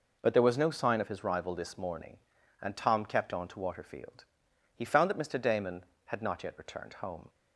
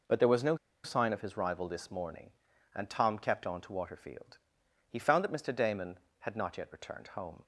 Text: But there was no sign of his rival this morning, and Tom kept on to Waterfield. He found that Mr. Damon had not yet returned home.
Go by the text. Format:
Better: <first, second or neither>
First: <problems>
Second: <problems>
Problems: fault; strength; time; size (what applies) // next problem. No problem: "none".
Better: first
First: none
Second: pauses between "no" and "sign"; slight; at 0.5 s; 0.27 s long